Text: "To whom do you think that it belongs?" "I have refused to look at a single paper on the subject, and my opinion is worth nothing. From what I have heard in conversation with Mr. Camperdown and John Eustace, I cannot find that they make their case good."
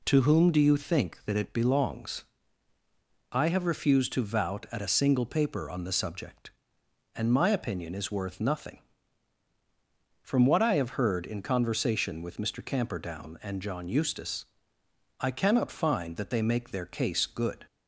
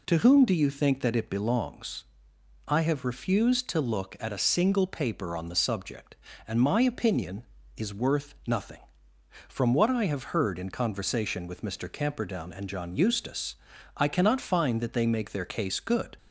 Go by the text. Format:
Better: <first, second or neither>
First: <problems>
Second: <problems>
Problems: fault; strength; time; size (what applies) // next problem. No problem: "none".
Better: second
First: says "vout" for "look"; at 4.2 s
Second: none